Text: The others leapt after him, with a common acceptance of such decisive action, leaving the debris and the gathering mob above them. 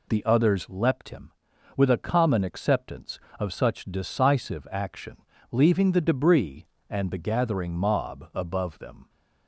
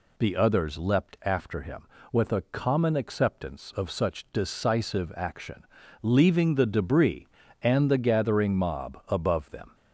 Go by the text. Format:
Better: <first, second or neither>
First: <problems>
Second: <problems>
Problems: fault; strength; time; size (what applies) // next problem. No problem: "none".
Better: second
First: skips "after"; at 1.0 s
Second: none